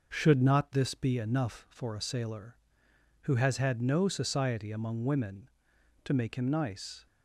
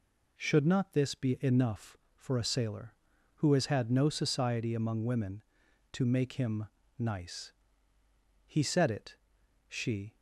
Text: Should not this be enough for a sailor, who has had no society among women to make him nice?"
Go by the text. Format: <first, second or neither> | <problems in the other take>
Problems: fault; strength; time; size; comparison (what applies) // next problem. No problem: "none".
first | pauses between "him" and "nice"; slight; at 6.6 s; 0.32 s long // goes on to say "He said it she"; strong; from 8.4 s on; 1.7 s long